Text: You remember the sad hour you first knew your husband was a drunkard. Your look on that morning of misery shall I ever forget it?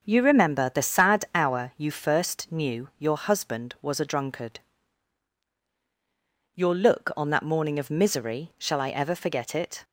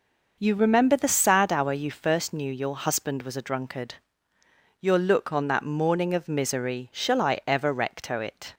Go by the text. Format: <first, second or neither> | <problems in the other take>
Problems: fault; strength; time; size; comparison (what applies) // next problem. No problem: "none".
first | says "recto" for "forget"; at 7.7 s